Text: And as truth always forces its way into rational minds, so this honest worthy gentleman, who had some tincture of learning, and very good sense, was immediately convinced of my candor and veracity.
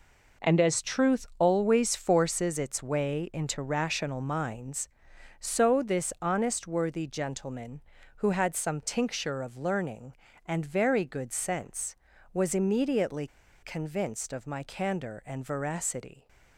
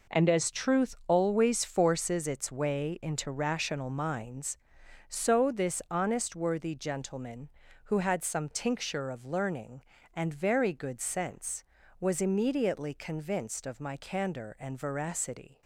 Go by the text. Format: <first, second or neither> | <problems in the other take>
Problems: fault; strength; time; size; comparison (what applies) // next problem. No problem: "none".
second | pauses between "immediately" and "convinced"; slight; at 13.2 s; 0.35 s long